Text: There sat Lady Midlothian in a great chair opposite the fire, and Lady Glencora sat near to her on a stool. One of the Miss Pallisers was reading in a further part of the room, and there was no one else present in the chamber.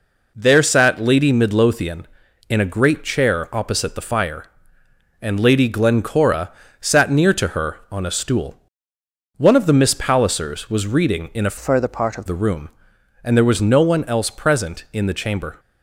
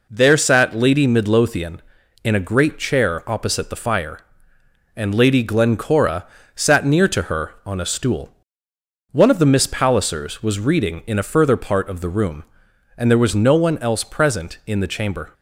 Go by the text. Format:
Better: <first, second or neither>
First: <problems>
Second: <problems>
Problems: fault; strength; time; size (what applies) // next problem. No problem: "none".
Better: second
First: pauses between "Glencora" and "sat"; slight; at 6.5 s; 0.30 s long // changes voice from "further" to "of"; from 11.5 to 12.2 s; 0.7 s long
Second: pauses between "Glencora" and "sat"; slight; at 6.2 s; 0.30 s long